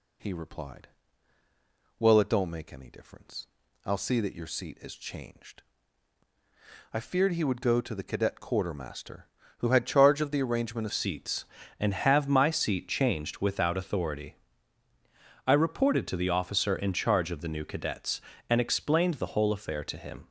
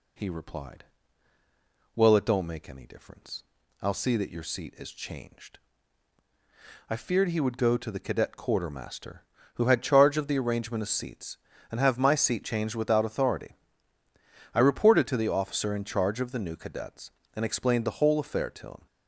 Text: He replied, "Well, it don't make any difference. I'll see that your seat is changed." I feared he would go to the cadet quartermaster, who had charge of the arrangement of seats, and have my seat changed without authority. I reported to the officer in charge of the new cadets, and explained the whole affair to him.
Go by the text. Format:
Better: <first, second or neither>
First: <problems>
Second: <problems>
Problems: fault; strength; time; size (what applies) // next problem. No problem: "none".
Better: second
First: changes voice at "seats"; from 10.9 s on; 9.3 s long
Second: none